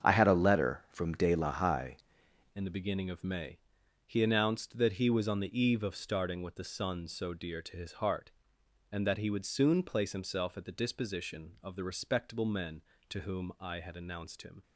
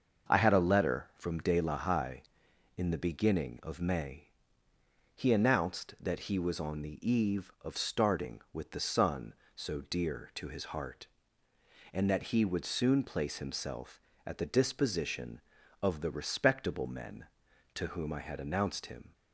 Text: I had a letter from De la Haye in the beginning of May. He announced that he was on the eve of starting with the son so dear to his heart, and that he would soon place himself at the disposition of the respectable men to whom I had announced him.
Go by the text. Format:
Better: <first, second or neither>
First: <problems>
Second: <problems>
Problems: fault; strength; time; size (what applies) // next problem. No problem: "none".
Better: second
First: starts louder than the rest; strong; until 1.1 s; 7.5 dB // changes voice at "in"; from 2.5 s on; 12.1 s long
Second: starts louder than the rest; until 1.3 s; 6.5 dB